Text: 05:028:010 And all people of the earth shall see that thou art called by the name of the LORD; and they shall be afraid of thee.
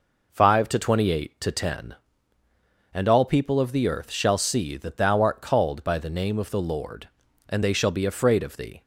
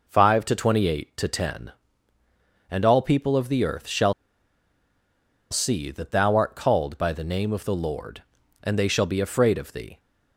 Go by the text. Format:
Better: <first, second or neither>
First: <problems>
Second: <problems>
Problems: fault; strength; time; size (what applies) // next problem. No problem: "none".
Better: first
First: none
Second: pauses between "shall" and "see"; strong; at 4.1 s; 1.3 s long